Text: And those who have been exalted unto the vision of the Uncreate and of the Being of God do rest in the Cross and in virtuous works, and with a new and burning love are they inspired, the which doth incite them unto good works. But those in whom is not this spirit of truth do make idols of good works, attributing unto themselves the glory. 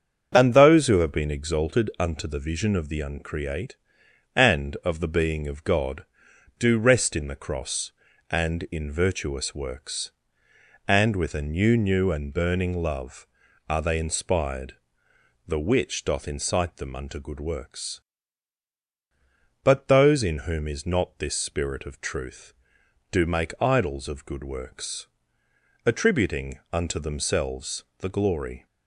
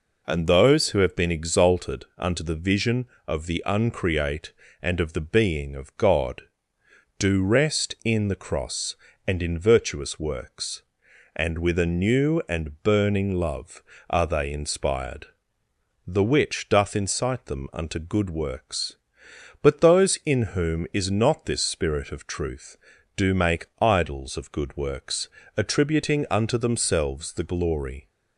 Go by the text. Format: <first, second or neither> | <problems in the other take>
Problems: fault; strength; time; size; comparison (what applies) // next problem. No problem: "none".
second | starts louder than the rest; strong; until 1.3 s; 7.5 dB // says "new" twice; at 11.7 s // pauses between "themselves" and "the"; slight; at 27.8 s; 0.16 s long